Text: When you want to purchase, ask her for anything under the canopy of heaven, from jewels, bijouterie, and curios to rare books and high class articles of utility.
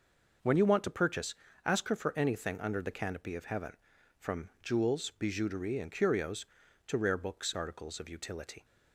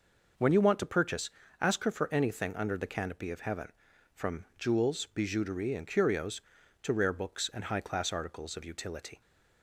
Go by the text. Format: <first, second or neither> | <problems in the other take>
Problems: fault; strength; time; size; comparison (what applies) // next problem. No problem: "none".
second | skips "and high class"; at 7.5 s